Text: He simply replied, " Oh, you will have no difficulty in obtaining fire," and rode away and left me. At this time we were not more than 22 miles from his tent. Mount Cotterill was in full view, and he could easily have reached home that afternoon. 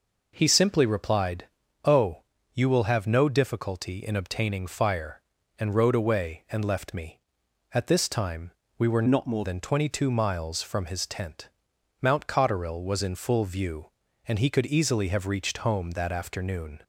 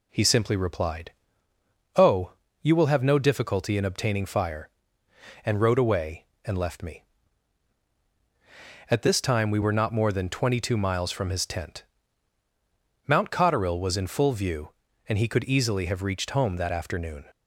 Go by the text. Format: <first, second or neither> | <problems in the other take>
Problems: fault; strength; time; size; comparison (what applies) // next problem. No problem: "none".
second | pauses between "time" and "we"; slight; at 8.5 s; 0.26 s long // changes voice from "not" to "more"; from 9.0 to 9.4 s; 0.4 s long